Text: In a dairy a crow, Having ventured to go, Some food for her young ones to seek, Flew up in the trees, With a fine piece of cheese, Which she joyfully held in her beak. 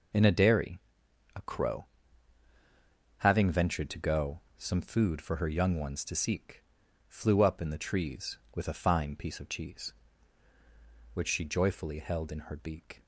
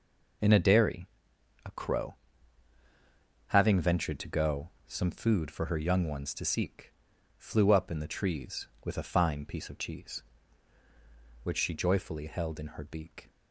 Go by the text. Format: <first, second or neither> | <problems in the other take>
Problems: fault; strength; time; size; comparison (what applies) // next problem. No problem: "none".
neither | pauses between "dairy" and "a"; noticeable; the same in both